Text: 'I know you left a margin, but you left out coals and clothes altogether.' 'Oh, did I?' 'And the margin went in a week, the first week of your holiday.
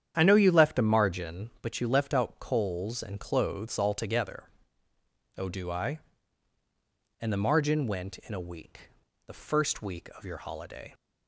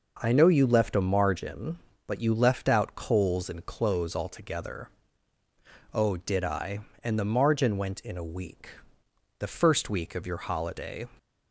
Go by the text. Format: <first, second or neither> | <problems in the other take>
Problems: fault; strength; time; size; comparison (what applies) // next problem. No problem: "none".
second | starts louder than the rest; strong; until 1.1 s; 9 dB // says "do" for "did"; at 5.4 s